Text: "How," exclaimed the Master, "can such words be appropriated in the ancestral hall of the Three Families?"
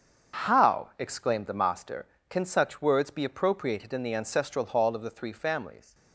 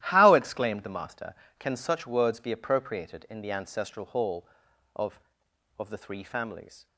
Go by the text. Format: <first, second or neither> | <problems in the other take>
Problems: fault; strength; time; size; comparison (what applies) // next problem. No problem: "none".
first | starts louder than the rest; strong; until 1.0 s; 13.5 dB; also in the first // says "of" twice; at 5.7 s